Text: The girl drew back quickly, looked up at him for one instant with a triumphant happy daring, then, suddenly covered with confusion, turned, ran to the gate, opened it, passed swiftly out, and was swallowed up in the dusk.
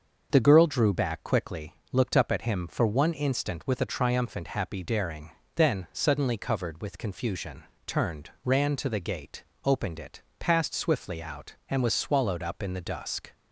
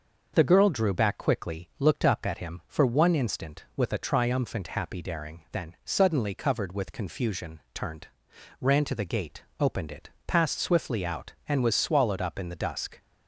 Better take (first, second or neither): neither